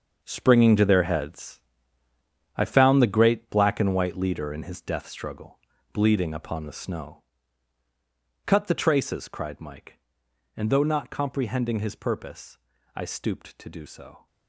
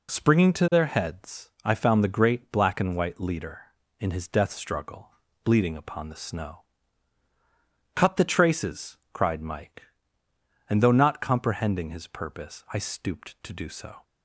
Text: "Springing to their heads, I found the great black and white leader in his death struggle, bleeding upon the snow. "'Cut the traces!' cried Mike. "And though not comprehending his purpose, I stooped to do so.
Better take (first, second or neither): second